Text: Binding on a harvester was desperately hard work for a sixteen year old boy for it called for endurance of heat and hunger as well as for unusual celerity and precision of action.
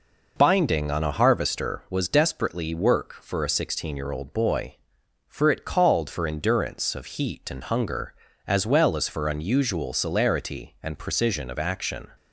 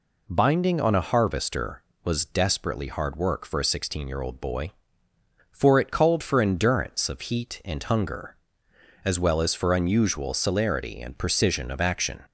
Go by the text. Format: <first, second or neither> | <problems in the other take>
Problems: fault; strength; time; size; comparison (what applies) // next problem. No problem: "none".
second | skips "hard"; at 2.7 s